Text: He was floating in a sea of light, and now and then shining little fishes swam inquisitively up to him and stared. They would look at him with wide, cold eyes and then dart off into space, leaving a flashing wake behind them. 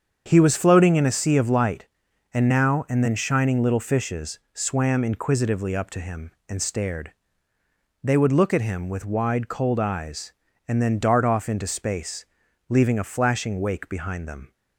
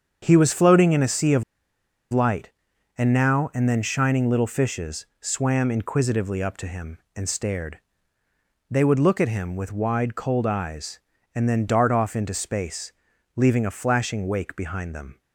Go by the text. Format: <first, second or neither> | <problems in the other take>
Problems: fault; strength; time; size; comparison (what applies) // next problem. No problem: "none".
first | starts louder than the rest; strong; until 1.2 s; 7 dB; strong in the first // pauses between "of" and "light"; noticeable; at 1.4 s; 0.69 s long // pauses between "fishes" and "swam"; slight; at 5.0 s; 0.16 s long; slight in the first